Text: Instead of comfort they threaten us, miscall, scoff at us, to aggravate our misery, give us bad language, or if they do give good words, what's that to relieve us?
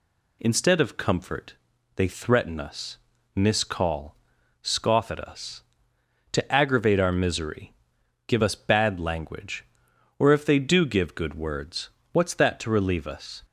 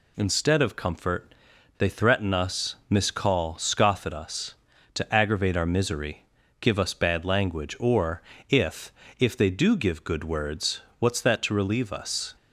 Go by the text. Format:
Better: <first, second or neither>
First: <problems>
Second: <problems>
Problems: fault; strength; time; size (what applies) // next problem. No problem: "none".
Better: first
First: pauses between "comfort" and "they"; at 1.5 s; 0.40 s long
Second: pauses between "comfort" and "they"; noticeable; at 1.3 s; 0.46 s long // pauses between "or" and "if"; slight; at 8.2 s; 0.28 s long // says "if" twice; at 9.1 s